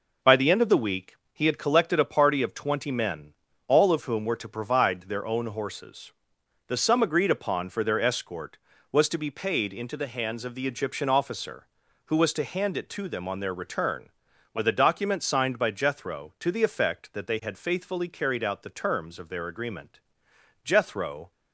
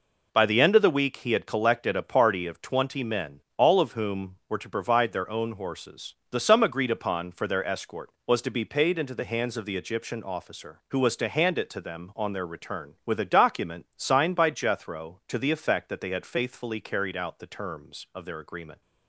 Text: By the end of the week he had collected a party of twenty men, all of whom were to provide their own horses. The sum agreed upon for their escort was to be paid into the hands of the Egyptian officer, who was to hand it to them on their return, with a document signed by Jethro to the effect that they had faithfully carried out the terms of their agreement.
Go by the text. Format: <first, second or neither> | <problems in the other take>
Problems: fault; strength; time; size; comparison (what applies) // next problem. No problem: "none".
second | pauses between "week" and "he"; slight; at 1.1 s; 0.18 s long // goes on to say "Jethro"; noticeable; from 20.6 s on; 0.68 s long